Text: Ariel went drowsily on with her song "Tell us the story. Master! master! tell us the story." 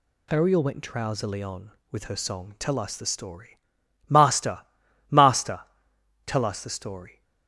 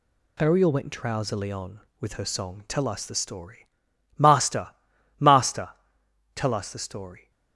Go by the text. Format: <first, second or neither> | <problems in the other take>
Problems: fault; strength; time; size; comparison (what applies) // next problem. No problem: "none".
first | gets quieter; noticeable; throughout; 4.5 dB